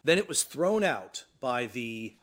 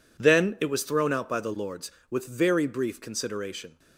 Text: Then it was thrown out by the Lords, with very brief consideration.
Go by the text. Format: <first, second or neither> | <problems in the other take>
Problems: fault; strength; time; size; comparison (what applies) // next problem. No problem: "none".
second | stops before "Lords with very brief consideration"; at 2.1 s